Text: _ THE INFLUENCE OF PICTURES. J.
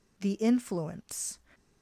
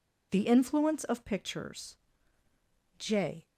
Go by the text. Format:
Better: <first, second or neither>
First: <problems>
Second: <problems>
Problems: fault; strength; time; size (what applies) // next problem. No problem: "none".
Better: second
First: stops before "OF PICTURES J"; at 1.5 s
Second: none